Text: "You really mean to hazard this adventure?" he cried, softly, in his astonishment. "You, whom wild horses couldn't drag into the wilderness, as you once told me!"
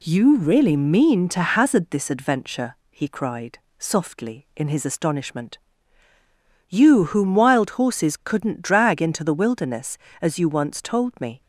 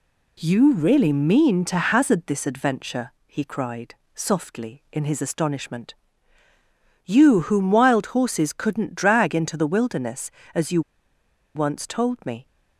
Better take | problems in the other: first | pauses between "you" and "once"; noticeable; at 10.8 s; 0.74 s long

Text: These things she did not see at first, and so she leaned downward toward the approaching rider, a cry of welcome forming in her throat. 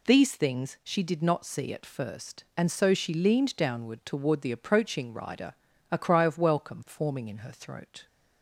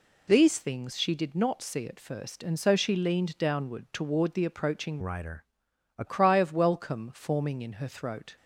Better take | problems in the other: first | changes voice from "rider" to "a"; from 5.0 to 6.0 s; 1.0 s long

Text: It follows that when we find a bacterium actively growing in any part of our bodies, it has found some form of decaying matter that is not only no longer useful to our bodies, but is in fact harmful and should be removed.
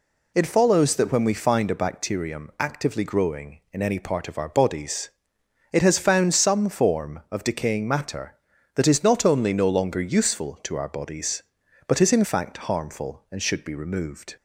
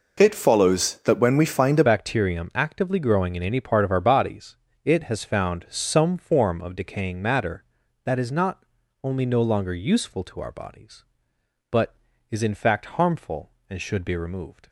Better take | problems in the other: first | changes voice at "bacterium"; from 1.8 s on; 12.8 s long // pauses between "not" and "only"; at 8.6 s; 0.38 s long

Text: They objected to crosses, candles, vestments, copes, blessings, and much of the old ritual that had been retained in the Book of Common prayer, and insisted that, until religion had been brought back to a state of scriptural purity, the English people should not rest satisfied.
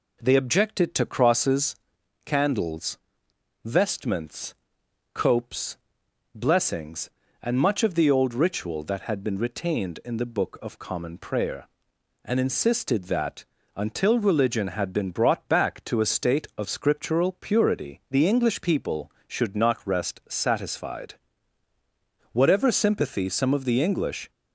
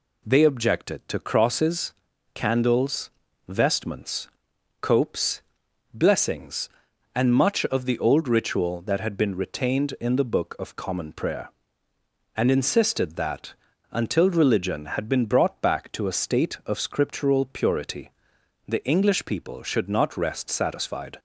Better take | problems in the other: second | goes on to say "Whatever sympathy some of the English"; strong; from 22.3 s on; 1.9 s long

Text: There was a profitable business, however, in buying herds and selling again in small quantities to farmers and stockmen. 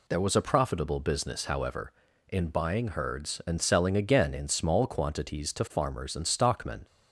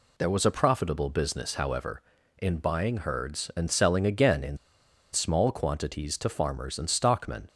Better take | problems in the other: first | pauses between "in" and "small"; noticeable; at 4.5 s; 0.56 s long

